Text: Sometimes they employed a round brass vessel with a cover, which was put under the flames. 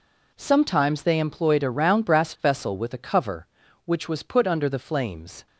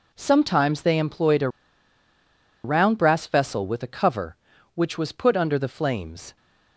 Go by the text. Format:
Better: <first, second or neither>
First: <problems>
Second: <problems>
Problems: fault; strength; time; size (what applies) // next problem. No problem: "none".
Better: first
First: none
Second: pauses between "a" and "round"; at 1.4 s; 1.1 s long